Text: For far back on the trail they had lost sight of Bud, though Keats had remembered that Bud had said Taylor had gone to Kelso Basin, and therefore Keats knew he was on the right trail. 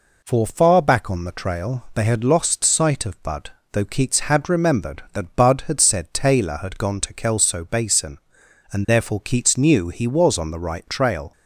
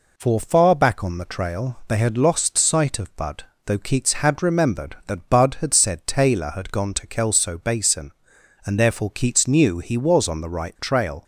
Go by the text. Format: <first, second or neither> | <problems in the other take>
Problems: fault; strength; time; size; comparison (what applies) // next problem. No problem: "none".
neither | none